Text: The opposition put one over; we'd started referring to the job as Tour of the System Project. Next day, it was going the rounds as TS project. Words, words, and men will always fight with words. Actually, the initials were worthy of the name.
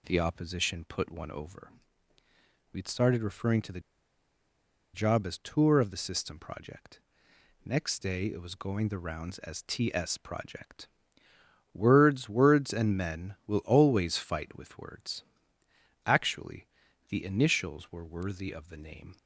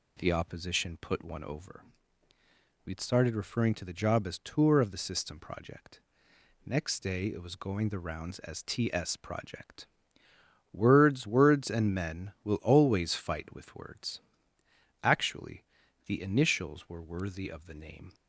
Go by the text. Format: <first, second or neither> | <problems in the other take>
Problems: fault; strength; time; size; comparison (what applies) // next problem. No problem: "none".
second | pauses between "the" and "job"; at 3.8 s; 1.1 s long